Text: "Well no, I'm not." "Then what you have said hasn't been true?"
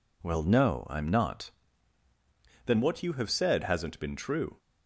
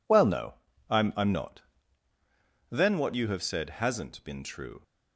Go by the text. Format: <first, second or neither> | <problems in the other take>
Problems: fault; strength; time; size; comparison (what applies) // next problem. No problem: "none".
first | says "I'm" twice; at 1.1 s